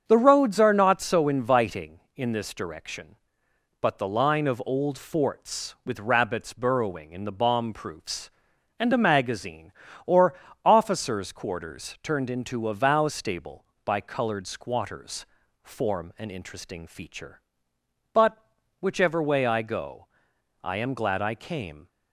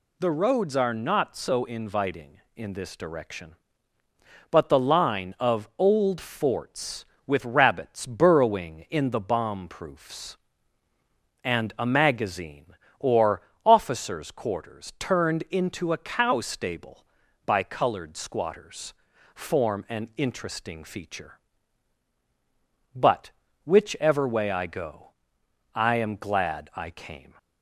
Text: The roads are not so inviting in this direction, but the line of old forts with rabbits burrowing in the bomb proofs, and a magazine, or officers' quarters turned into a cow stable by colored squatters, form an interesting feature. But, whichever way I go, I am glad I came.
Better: second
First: starts louder than the rest; strong; until 1.0 s; 7.5 dB // pauses between "or" and "officers"; slight; at 10.3 s; 0.28 s long // says "vow" for "cow"; at 12.7 s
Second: pauses between "or" and "officers"; slight; at 13.4 s; 0.22 s long

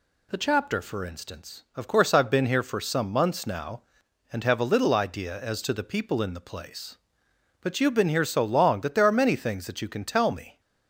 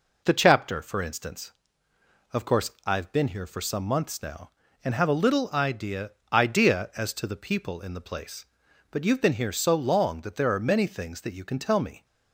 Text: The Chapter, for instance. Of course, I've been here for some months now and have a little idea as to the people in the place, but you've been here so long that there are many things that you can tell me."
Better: first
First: none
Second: says "idea" twice; at 6.3 s

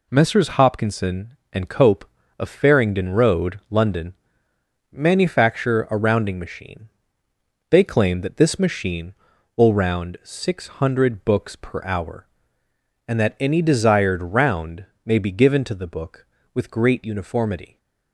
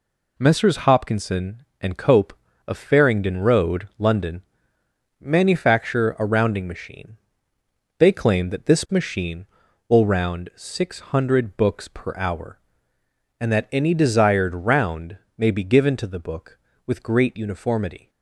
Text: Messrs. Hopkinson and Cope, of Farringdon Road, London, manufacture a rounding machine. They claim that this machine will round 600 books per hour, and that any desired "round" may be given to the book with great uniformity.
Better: neither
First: pauses between "round" and "may"; slight; at 14.8 s; 0.18 s long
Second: pauses between "round" and "may"; slight; at 15.1 s; 0.18 s long

